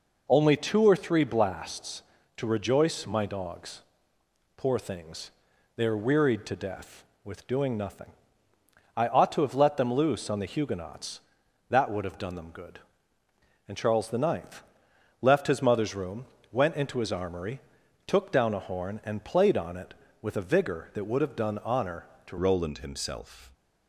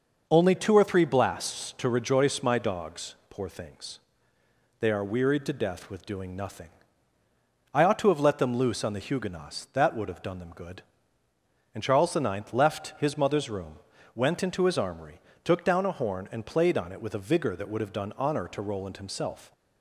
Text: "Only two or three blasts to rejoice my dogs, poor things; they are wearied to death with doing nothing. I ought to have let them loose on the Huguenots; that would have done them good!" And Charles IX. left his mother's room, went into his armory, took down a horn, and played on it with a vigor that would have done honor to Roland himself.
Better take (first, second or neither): second